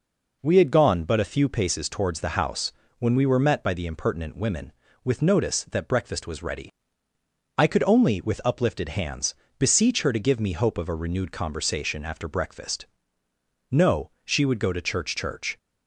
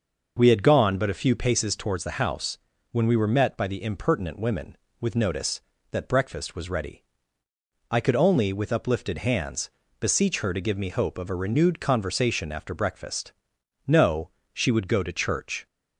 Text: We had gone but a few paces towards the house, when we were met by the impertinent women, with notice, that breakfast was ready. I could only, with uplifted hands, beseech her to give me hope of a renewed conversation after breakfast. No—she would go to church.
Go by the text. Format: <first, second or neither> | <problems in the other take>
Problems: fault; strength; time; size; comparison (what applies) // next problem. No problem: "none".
second | says "church" twice; at 15.1 s